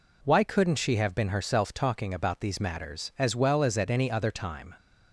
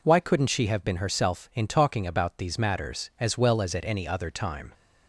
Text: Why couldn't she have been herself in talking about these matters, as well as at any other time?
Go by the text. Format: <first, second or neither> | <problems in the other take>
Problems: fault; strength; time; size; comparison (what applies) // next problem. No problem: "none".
second | skips "in"; at 1.7 s